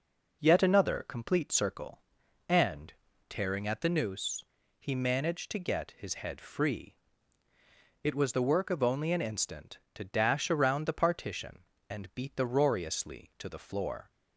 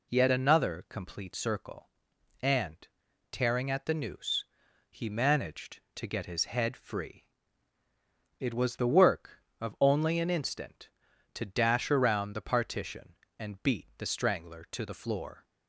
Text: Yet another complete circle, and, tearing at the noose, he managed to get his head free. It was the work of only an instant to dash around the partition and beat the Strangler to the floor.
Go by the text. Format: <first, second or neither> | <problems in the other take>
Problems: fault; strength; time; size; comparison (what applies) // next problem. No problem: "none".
second | says "Roariously" for "Strangler"; at 12.4 s